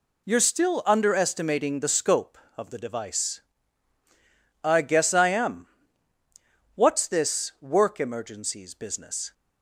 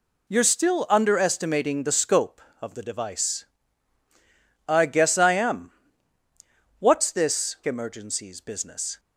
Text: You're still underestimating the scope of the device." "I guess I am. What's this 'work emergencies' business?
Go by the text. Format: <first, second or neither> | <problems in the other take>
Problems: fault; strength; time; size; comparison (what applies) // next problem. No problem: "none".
first | skips "work"; at 7.6 s